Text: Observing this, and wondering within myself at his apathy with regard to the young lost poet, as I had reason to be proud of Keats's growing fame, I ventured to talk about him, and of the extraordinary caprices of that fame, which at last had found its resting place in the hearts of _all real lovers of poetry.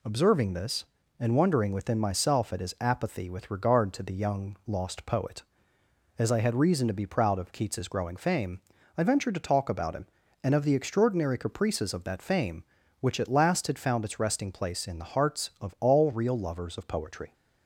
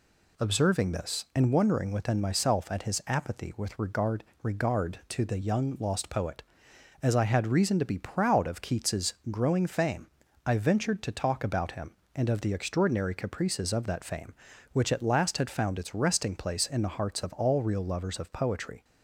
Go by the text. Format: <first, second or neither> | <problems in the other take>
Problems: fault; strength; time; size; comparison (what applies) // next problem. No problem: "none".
first | says "regard" twice; at 4.4 s // pauses between "Keats's" and "growing"; slight; at 9.1 s; 0.16 s long